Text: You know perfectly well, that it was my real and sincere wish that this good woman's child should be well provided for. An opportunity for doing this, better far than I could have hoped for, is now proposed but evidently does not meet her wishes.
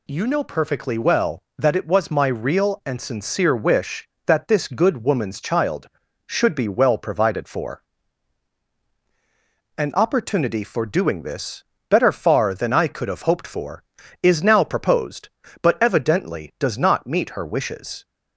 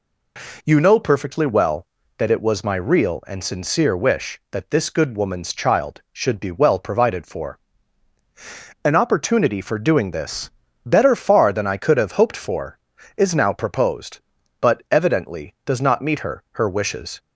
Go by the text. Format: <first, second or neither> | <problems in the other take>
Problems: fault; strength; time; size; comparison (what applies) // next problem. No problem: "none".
first | says "her" twice; at 16.5 s